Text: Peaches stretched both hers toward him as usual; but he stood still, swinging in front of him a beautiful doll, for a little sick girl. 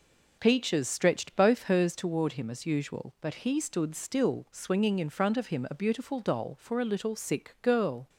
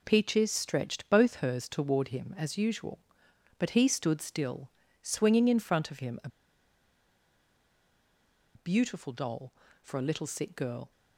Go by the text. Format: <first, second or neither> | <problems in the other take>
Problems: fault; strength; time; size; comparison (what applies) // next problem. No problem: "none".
first | pauses between "a" and "beautiful"; strong; at 6.2 s; 2.2 s long